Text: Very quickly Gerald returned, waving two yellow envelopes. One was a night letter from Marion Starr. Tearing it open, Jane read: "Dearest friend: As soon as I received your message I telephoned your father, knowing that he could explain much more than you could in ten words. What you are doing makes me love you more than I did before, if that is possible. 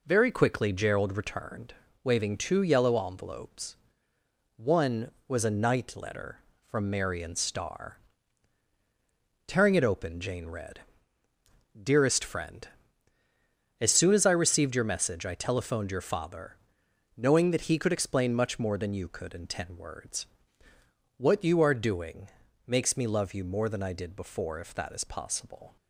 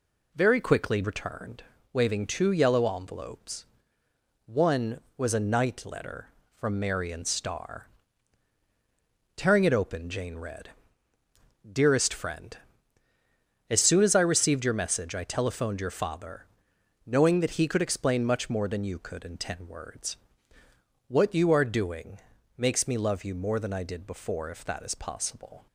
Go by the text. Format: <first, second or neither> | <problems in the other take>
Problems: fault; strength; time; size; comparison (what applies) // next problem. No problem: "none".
first | skips "Gerald"; at 1.0 s // pauses between "doing" and "makes"; at 22.1 s; 0.38 s long; also in the first